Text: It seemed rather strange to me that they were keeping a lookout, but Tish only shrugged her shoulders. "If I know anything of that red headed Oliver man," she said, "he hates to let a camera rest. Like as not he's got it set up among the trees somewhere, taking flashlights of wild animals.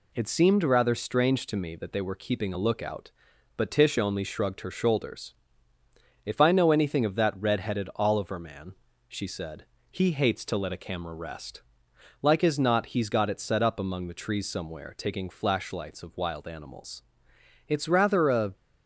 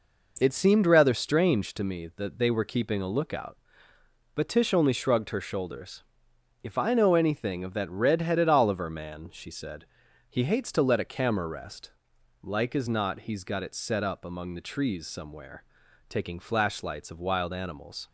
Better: second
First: goes on to say "It's rather a"; noticeable; from 17.6 s on; 0.86 s long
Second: none

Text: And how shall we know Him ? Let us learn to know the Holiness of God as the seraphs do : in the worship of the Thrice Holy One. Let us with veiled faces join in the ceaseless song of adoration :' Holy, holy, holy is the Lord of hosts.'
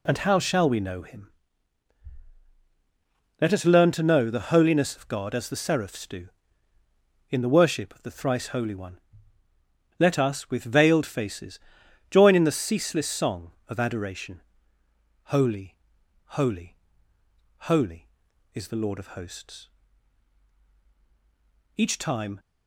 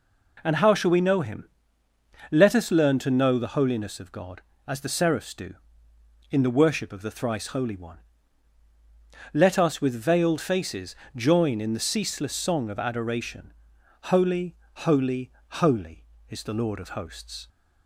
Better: second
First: pauses between "faces" and "join"; noticeable; at 11.5 s; 0.50 s long // goes on to say "Each time"; noticeable; from 21.7 s on; 0.62 s long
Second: pauses between "faces" and "join"; slight; at 10.9 s; 0.22 s long

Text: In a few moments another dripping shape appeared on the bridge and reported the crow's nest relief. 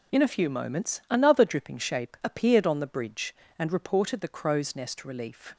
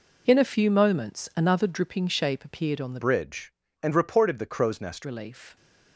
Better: first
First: none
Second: changes voice from "bridge" to "nest"; from 3.0 to 5.0 s; 2.0 s long

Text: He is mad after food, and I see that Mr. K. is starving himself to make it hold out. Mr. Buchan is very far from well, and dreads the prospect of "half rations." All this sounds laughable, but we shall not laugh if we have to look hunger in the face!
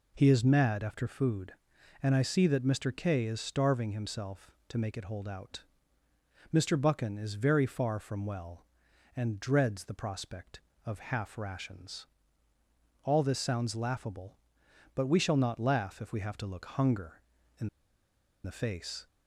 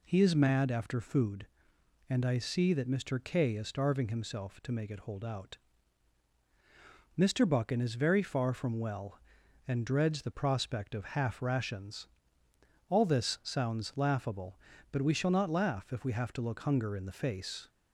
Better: second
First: pauses between "in" and "the"; noticeable; at 17.6 s; 0.77 s long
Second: none

